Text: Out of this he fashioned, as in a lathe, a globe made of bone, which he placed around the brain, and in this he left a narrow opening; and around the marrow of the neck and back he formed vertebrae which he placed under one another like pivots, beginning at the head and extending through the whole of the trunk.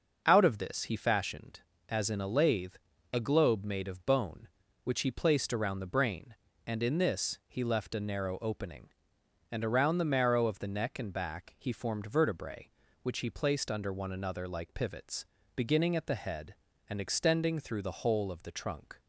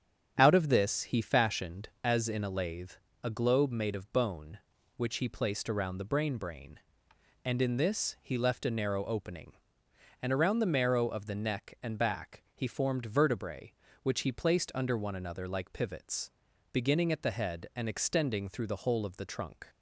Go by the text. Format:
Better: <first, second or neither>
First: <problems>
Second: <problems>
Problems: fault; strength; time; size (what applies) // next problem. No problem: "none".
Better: first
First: starts louder than the rest; until 1.2 s; 6 dB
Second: starts louder than the rest; strong; until 1.3 s; 8 dB // says "brain" twice; at 6.3 s